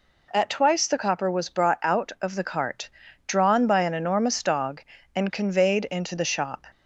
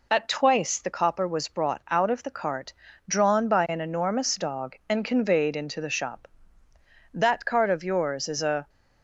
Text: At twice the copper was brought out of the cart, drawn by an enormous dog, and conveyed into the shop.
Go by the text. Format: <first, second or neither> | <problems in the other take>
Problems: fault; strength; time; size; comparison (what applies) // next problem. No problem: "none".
first | goes on to say "That cart of yours is a"; from 7.1 s on; 1.5 s long